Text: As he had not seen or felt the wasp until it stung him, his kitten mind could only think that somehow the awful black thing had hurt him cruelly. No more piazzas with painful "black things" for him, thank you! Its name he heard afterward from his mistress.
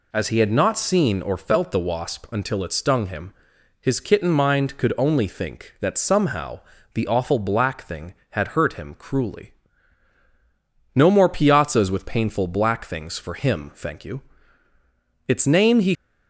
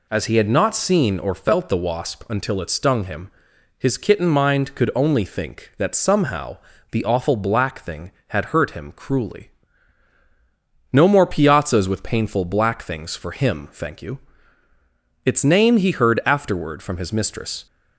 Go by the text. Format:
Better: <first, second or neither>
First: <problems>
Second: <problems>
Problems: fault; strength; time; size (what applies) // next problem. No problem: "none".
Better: second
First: pauses between "somehow" and "the"; slight; at 6.6 s; 0.34 s long // stops before "heard afterward from his mistress"; at 15.9 s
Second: pauses between "somehow" and "the"; slight; at 6.5 s; 0.34 s long